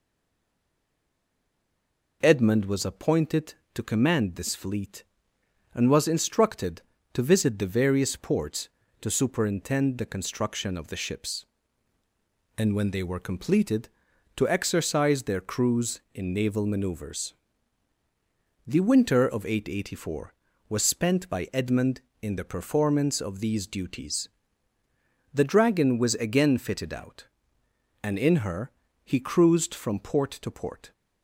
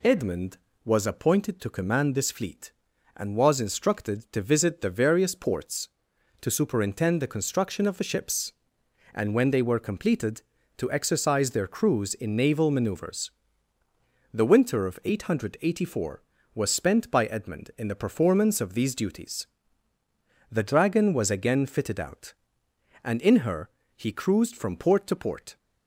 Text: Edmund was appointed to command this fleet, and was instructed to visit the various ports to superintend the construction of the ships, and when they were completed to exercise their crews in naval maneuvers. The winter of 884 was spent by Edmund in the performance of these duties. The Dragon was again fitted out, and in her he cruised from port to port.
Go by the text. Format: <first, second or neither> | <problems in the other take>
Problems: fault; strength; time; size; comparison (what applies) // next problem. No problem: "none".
second | stays silent before the first word; until 2.2 s; 2.2 s long // pauses between "her" and "he"; slight; at 28.7 s; 0.34 s long; slight in the second